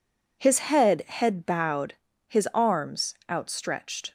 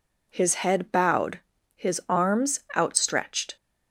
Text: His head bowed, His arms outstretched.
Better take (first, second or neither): second